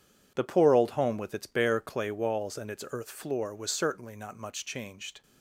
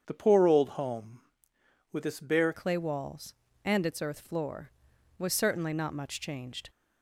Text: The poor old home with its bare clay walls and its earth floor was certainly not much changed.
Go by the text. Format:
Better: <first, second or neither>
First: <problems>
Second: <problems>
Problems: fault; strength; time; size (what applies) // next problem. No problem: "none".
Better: first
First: none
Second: starts louder than the rest; strong; until 1.0 s; 7.5 dB // changes voice at "clay"; from 2.5 s on; 4.1 s long